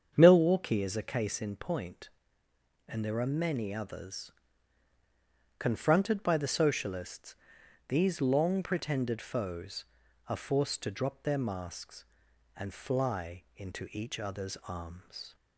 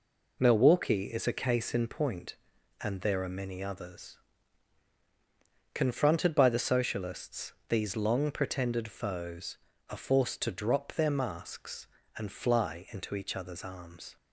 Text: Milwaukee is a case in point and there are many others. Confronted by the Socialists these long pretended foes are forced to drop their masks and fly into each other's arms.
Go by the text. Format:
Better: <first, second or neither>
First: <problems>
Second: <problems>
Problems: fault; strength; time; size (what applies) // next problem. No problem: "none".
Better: second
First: starts louder than the rest; strong; until 1.3 s; 7.5 dB // pauses between "Socialists" and "these"; noticeable; at 7.3 s; 0.54 s long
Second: pauses between "Socialists" and "these"; slight; at 7.5 s; 0.16 s long